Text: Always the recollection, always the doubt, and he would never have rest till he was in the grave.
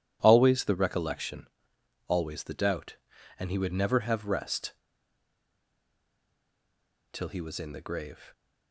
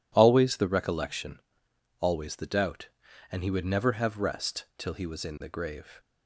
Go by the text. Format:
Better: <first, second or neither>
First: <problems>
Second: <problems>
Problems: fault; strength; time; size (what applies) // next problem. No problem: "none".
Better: second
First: pauses between "rest" and "till"; strong; at 4.7 s; 2.3 s long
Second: none